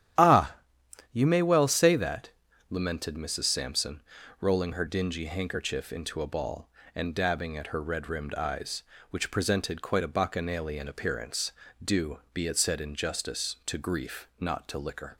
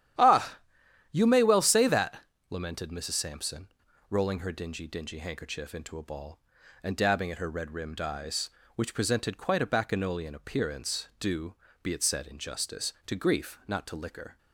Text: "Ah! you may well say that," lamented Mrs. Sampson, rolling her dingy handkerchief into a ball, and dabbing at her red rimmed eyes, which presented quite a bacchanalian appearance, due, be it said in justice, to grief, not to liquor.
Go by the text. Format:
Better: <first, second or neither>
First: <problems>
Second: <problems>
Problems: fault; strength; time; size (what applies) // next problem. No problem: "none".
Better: first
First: starts louder than the rest; strong; until 1.7 s; 10.5 dB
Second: starts louder than the rest; strong; until 1.6 s; 10.5 dB // says "dingy" twice; at 4.8 s